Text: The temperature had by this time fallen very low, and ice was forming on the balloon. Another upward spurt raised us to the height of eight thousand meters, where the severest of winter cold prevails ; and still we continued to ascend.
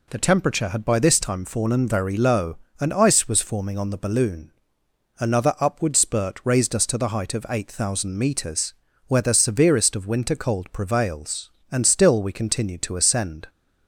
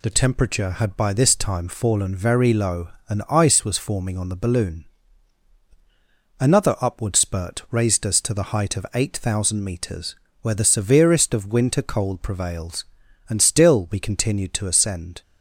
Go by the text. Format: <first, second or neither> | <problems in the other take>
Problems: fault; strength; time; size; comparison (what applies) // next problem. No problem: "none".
neither | none